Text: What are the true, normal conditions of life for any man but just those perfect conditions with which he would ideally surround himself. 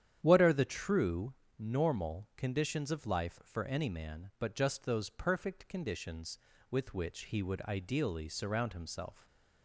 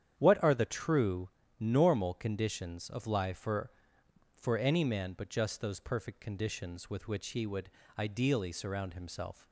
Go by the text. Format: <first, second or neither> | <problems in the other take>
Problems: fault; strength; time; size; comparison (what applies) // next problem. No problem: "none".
first | starts louder than the rest; strong; until 1.1 s; 9 dB; strong in the first // says "for" twice; at 4.3 s // pauses between "would" and "ideally"; slight; at 7.6 s; 0.30 s long